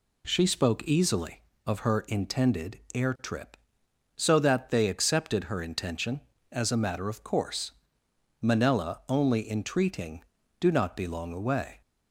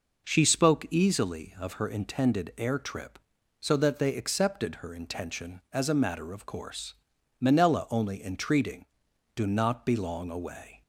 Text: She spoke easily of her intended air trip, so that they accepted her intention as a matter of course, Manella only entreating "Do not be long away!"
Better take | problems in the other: neither | none

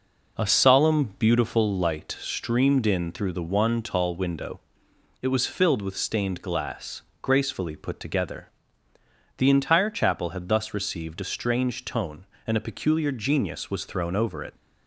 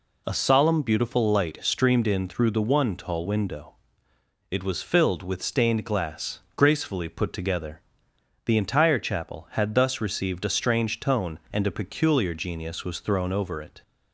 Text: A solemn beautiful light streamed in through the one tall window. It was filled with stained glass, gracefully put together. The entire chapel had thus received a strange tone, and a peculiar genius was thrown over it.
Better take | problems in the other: second | starts louder than the rest; noticeable; until 1.7 s; 5 dB

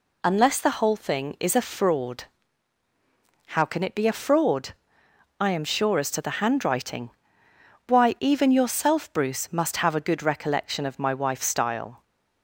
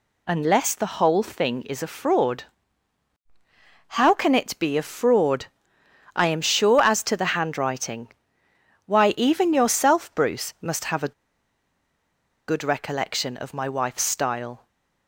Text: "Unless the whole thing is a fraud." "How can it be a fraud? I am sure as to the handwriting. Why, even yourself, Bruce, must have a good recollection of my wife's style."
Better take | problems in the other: first | pauses between "a" and "good"; strong; at 11.1 s; 1.3 s long

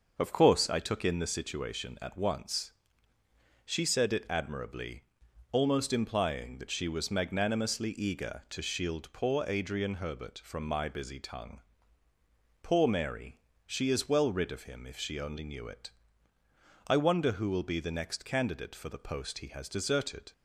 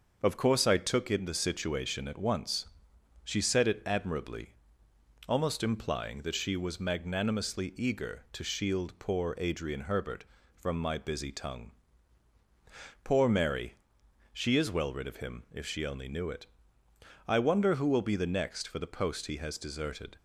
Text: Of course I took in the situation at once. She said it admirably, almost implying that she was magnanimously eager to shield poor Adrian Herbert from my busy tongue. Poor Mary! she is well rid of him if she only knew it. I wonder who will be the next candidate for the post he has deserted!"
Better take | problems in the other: first | starts louder than the rest; until 1.2 s; 6.5 dB; also in the first // skips "candidate"; at 18.6 s

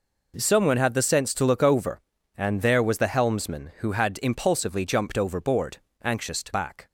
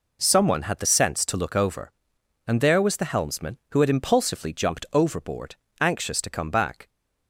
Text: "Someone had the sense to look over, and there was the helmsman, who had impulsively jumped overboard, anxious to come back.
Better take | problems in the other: second | skips "come"; at 6.5 s

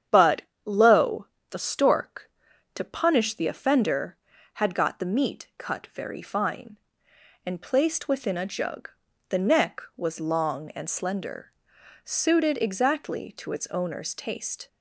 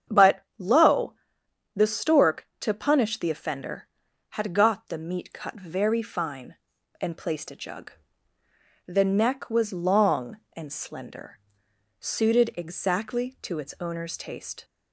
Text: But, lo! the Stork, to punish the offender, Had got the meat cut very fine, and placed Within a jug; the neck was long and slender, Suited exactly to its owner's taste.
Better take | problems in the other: first | starts louder than the rest; strong; until 1.8 s; 8 dB; strong in the first // skips "Within"; at 7.5 s

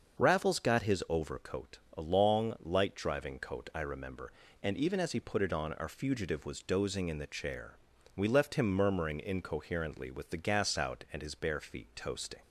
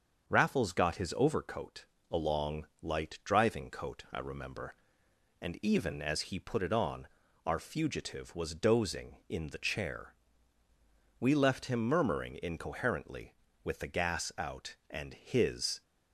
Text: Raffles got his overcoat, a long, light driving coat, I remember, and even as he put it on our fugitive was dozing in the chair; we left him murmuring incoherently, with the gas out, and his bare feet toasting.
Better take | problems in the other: first | starts louder than the rest; until 1.3 s; 6.5 dB; also in the first // pauses between "on" and "our"; slight; at 7.0 s; 0.36 s long // stops before "bare feet toasting"; at 15.8 s

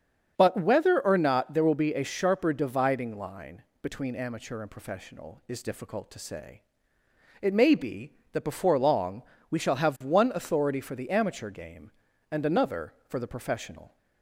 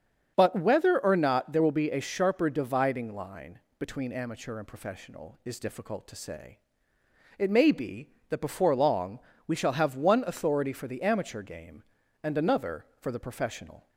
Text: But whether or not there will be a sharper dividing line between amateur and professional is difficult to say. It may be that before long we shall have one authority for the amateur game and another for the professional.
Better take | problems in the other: neither | starts louder than the rest; strong; the same in both // pauses between "line" and "between"; slight; the same in both // pauses between "long" and "we"; slight; the same in both

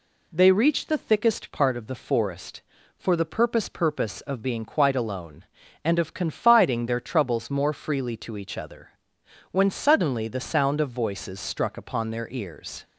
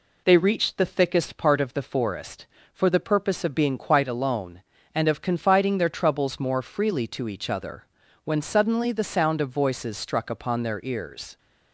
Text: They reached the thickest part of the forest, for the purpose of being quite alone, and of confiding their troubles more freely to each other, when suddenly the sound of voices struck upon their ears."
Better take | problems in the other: second | says "purpose" twice; at 3.6 s

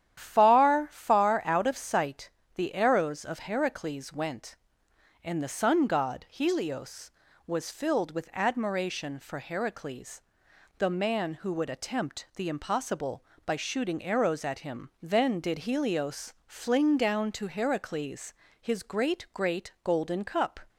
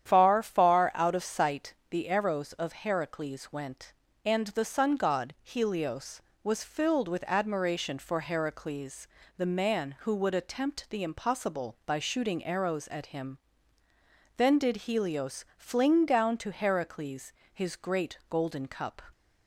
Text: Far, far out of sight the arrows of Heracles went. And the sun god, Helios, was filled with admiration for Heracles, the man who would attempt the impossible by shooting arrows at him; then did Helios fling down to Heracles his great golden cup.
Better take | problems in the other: second | starts louder than the rest; strong; until 1.1 s; 10.5 dB; strong in the second // pauses between "sight" and "the"; slight; at 2.2 s; 0.28 s long; slight in the second // pauses between "Helios" and "fling"; slight; at 16.3 s; 0.16 s long // pauses between "Heracles" and "his"; slight; at 18.3 s; 0.28 s long; slight in the second // says "great" twice; at 19.3 s

